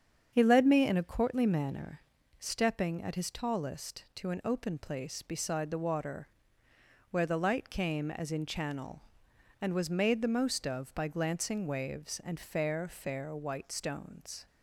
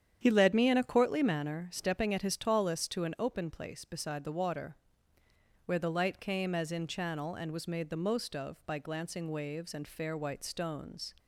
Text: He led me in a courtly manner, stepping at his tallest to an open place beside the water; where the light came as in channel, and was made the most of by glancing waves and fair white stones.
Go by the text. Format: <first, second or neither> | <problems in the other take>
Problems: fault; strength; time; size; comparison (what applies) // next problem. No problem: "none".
second | starts louder than the rest; strong; until 1.3 s; 7.5 dB; strong in the second // says "fair" twice; at 12.8 s